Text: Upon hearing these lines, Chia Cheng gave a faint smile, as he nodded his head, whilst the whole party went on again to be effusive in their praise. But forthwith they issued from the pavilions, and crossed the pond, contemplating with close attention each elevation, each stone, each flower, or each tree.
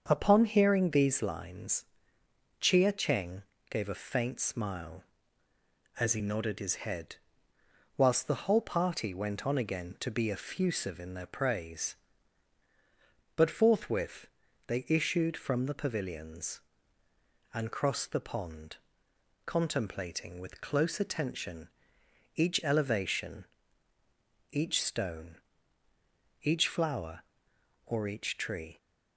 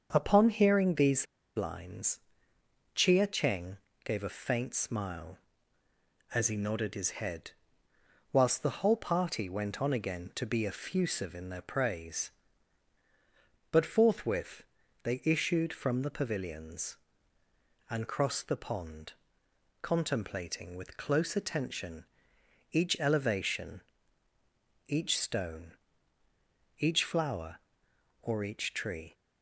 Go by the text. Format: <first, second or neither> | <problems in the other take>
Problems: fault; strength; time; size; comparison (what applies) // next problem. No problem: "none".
first | starts louder than the rest; until 1.1 s; 6.5 dB; also in the first // pauses between "these" and "lines"; slight; at 1.2 s; 0.31 s long // pauses between "Cheng" and "gave"; slight; at 3.7 s; 0.26 s long; slight in the first // pauses between "forthwith" and "they"; at 14.6 s; 0.40 s long; also in the first // pauses between "attention" and "each"; noticeable; at 22.0 s; 0.68 s long; noticeable in the first